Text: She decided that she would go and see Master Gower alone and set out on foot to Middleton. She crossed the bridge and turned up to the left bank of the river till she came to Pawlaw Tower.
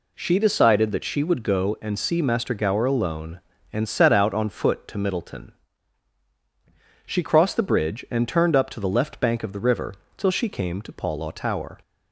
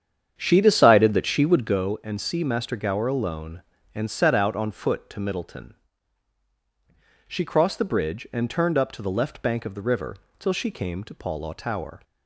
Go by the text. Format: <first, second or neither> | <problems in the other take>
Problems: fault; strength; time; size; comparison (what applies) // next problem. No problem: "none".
first | starts louder than the rest; strong; until 1.8 s; 8 dB // pauses between "river" and "till"; slight; at 10.1 s; 0.24 s long; slight in the first